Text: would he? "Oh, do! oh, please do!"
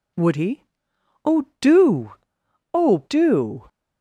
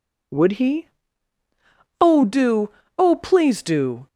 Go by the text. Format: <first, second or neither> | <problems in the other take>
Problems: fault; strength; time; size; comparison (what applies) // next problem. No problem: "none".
second | skips "please"; at 3.0 s